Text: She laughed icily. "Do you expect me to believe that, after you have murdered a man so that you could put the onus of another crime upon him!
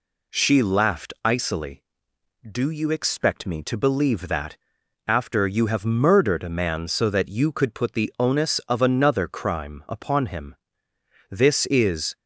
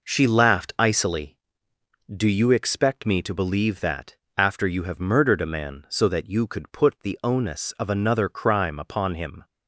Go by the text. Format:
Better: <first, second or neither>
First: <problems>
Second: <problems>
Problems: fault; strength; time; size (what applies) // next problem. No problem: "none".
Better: second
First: goes on to say "This is"; noticeable; from 11.2 s on; 0.86 s long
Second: none